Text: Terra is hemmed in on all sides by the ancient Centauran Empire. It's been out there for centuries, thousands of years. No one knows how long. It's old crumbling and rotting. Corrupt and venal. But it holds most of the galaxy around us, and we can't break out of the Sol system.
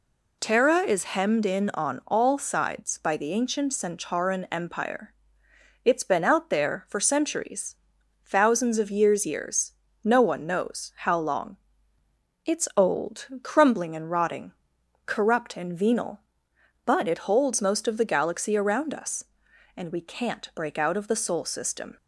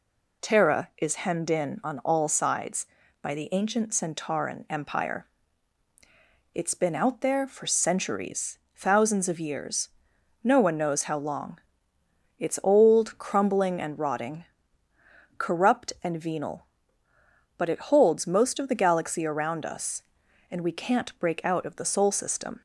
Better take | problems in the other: second | says "years" twice; at 9.2 s // pauses between "old" and "crumbling"; slight; at 13.2 s; 0.16 s long

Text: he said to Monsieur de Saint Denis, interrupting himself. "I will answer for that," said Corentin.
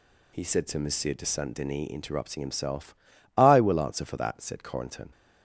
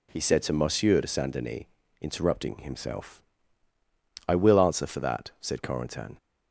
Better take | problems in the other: neither | none

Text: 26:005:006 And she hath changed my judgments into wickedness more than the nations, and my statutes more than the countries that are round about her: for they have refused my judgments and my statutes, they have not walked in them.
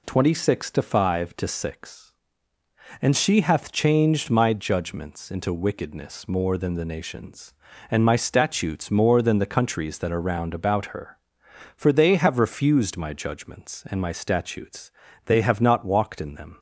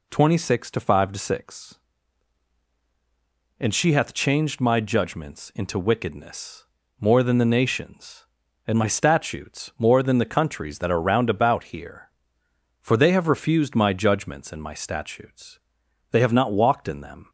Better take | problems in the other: first | pauses between "wickedness" and "more"; slight; at 6.6 s; 0.34 s long // says "here" for "her"; at 11.6 s

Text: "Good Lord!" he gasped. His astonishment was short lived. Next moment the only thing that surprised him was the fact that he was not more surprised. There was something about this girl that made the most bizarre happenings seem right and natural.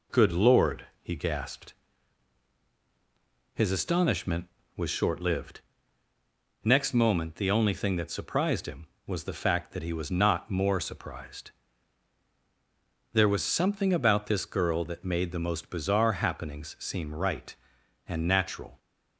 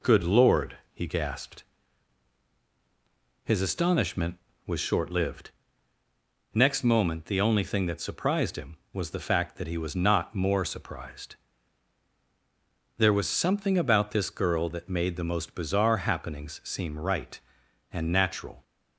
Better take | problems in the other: neither | none

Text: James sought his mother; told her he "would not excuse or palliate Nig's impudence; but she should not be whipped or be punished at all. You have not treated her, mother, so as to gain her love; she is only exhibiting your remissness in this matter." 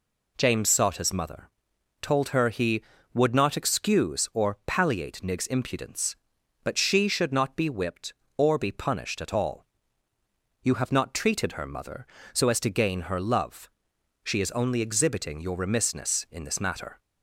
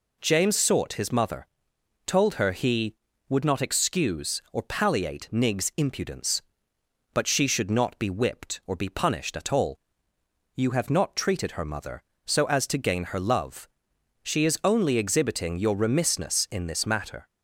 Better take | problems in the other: neither | none

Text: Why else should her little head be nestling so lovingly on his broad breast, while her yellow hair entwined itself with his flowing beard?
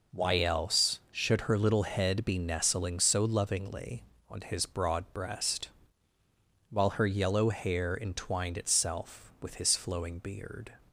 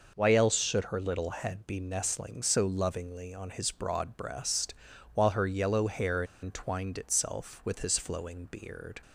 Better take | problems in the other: first | pauses between "hair" and "entwined"; slight; at 6.2 s; 0.19 s long

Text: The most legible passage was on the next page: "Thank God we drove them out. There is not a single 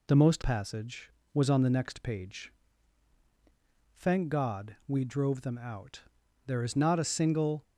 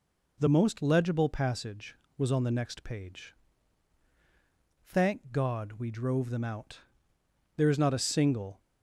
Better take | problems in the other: second | skips "legible"; at 0.4 s

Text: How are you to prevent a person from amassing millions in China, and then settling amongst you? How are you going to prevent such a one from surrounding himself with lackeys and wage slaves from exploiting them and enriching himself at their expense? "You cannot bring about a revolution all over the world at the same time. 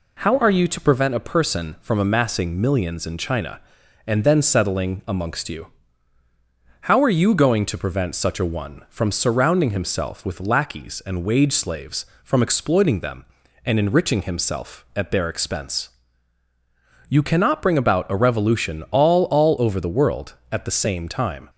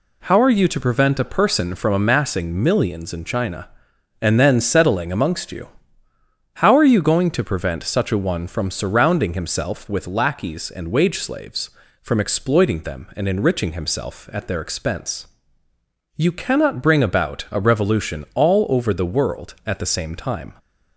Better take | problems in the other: second | says "all" twice; at 19.2 s

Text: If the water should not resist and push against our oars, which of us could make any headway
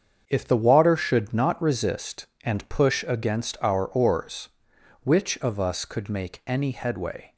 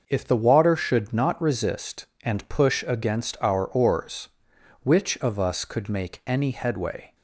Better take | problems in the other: second | gets quieter; strong; throughout; 9.5 dB

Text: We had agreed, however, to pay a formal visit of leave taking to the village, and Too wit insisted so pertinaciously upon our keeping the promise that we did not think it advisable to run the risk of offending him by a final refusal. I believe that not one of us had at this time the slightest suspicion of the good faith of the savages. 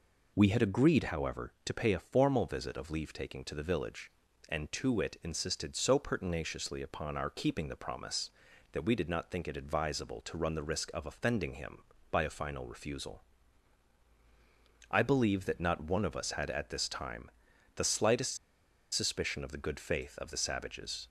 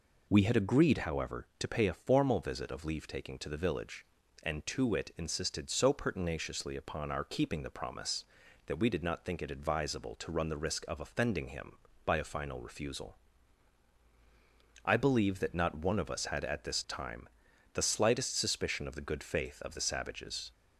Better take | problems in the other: second | pauses between "time" and "the"; noticeable; at 17.2 s; 0.46 s long; noticeable in the second // pauses between "slightest" and "suspicion"; noticeable; at 18.3 s; 0.56 s long

